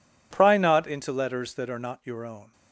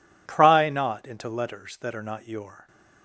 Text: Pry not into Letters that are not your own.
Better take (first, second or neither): first